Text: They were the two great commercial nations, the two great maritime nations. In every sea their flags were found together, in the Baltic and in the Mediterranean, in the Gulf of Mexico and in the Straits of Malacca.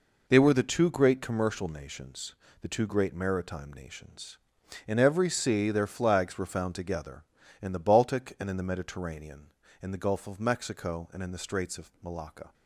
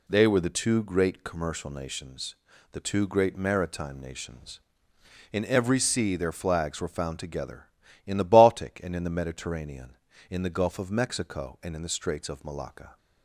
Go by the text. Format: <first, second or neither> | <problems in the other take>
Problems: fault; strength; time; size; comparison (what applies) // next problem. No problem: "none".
neither | none